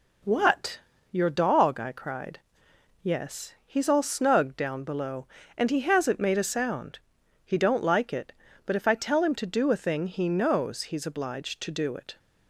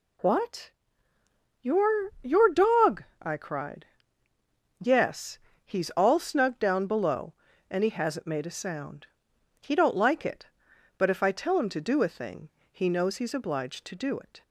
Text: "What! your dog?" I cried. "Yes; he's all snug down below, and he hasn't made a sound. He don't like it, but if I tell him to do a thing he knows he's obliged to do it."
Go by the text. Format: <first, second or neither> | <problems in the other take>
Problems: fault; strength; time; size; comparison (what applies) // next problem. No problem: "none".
first | says "your" twice; at 2.2 s // pauses between "thing" and "he"; slight; at 12.5 s; 0.20 s long